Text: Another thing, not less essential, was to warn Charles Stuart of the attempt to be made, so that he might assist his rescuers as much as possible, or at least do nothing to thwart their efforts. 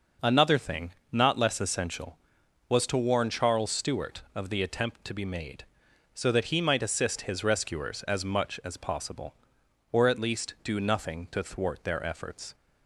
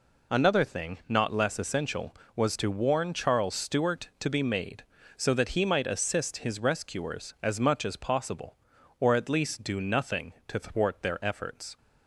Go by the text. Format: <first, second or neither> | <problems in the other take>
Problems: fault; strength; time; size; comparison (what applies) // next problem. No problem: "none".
first | skips "of the attempt"; at 4.1 s